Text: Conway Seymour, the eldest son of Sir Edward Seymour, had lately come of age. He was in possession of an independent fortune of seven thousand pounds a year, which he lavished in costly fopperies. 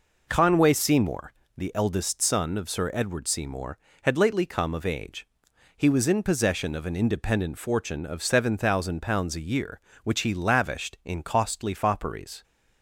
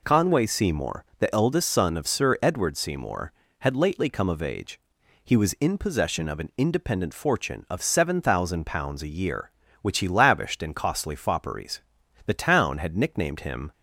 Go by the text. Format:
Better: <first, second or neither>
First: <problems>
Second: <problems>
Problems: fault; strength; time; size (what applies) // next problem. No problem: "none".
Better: first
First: none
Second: goes on to say "The town had nicknamed him"; from 12.2 s on; 1.4 s long